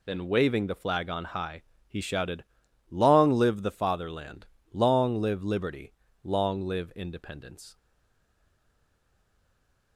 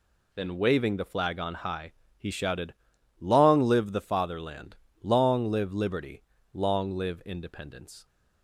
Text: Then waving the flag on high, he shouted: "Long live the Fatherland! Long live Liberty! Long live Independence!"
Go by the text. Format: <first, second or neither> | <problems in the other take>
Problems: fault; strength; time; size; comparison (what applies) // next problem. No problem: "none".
second | stays silent after the last word; from 7.7 s on; 2.2 s long